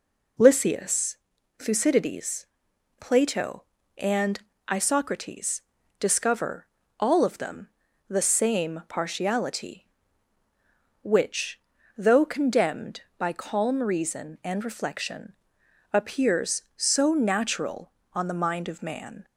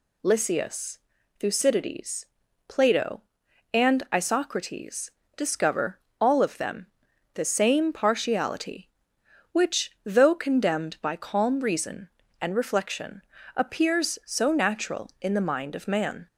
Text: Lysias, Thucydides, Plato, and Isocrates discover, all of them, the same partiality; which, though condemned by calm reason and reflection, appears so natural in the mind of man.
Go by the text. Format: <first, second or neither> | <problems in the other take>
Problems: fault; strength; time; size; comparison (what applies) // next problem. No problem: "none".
second | pauses between "and" and "Isocrates"; slight; at 4.3 s; 0.30 s long // pauses between "Isocrates" and "discover"; slight; at 5.6 s; 0.36 s long; slight in the second // says "on" for "in"; at 18.1 s